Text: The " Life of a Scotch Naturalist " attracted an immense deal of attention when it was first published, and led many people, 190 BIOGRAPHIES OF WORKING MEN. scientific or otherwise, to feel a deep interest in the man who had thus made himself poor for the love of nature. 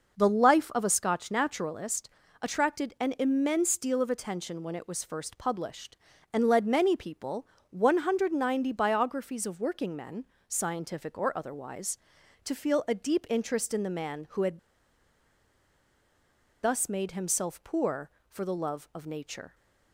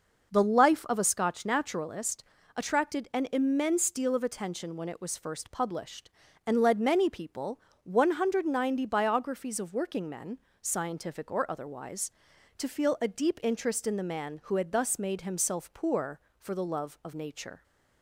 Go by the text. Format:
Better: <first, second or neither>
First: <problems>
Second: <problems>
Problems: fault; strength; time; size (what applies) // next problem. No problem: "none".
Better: second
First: pauses between "had" and "thus"; strong; at 14.5 s; 2.0 s long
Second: none